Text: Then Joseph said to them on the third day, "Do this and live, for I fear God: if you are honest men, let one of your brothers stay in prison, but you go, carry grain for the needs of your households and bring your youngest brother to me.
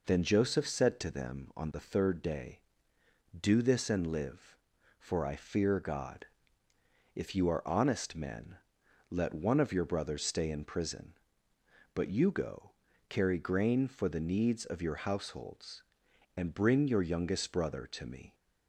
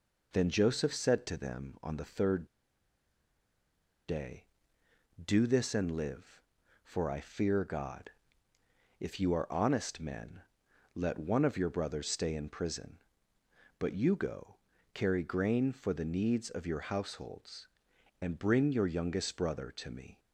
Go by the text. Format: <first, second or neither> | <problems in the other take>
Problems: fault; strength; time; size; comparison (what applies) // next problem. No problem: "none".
first | pauses between "third" and "day"; strong; at 2.4 s; 1.6 s long